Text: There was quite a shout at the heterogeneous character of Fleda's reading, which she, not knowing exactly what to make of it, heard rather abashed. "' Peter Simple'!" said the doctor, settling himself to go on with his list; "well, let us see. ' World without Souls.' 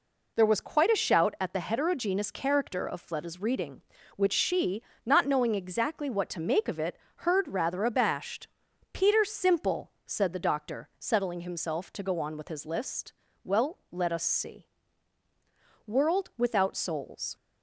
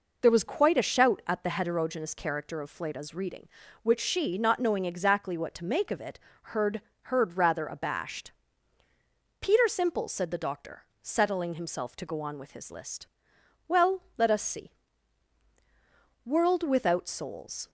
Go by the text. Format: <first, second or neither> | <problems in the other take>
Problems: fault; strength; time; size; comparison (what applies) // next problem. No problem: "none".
first | says "heard" twice; at 7.0 s